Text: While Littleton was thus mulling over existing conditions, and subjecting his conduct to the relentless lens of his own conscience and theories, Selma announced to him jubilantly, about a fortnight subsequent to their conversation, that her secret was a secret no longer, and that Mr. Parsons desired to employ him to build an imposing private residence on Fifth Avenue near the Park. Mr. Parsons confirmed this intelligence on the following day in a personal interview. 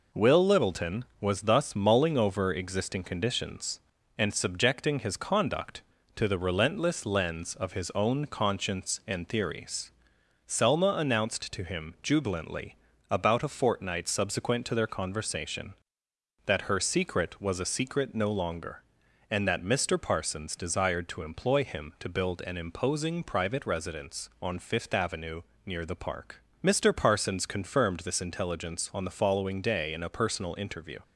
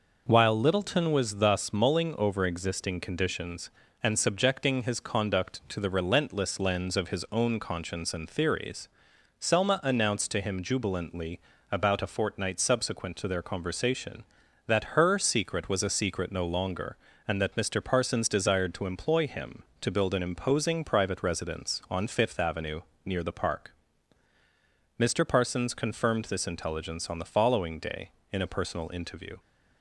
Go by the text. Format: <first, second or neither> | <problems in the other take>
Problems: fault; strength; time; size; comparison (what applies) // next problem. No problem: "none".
second | says "Will" for "While"; at 0.1 s // pauses between "Avenue" and "near"; slight; at 25.4 s; 0.24 s long; slight in the second